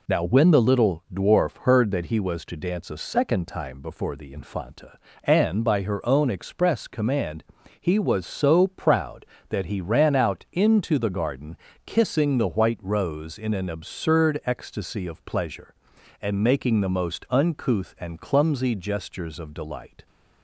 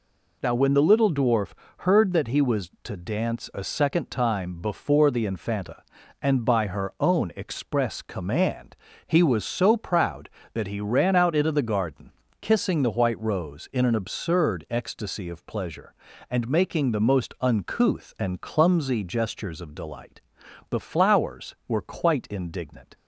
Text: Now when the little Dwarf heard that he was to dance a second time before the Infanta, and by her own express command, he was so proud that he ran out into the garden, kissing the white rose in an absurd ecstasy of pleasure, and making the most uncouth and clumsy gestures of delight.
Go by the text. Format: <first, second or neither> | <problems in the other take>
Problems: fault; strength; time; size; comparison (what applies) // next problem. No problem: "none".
first | pauses between "Dwarf" and "heard"; slight; at 1.5 s; 0.26 s long // goes on to say "The Flowers were quite indignant"; strong; from 20.6 s on; 2.2 s long